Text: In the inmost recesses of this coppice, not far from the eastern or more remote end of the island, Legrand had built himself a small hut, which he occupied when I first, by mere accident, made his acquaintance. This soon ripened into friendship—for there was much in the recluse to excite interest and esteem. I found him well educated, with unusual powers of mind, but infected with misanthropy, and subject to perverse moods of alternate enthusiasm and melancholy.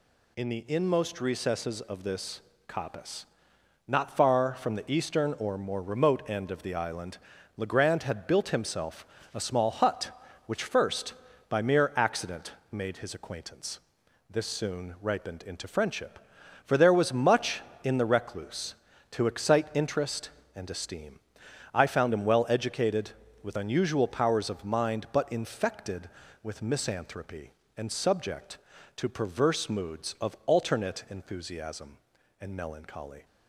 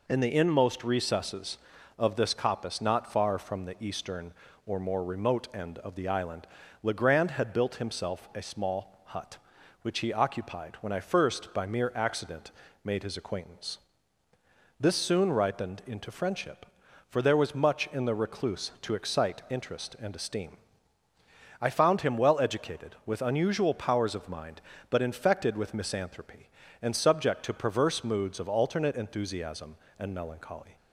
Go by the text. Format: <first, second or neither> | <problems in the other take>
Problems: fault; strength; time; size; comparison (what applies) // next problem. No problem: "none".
second | pauses between "this" and "coppice"; slight; at 2.4 s; 0.26 s long // pauses between "himself" and "a"; slight; at 9.0 s; 0.26 s long // skips "he occupied when I"; at 10.6 s